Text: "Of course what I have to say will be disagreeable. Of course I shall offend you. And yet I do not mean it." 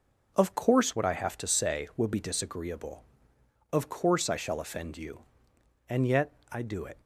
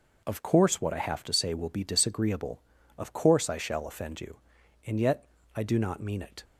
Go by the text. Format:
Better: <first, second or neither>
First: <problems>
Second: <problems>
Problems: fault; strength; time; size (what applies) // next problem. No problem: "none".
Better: second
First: pauses between "yet" and "I"; slight; at 6.3 s; 0.20 s long // skips "not mean"; at 6.8 s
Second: pauses between "yet" and "I"; slight; at 5.2 s; 0.30 s long